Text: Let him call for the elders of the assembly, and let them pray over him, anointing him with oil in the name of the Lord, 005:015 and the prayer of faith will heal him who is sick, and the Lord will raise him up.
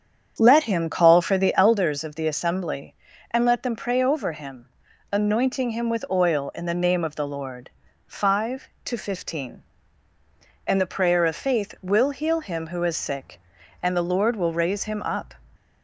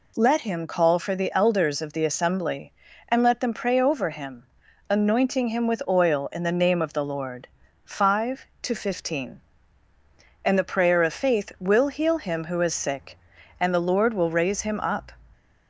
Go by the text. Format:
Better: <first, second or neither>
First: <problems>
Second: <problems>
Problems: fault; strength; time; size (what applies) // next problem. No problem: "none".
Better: second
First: starts louder than the rest; strong; until 1.8 s; 8 dB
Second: none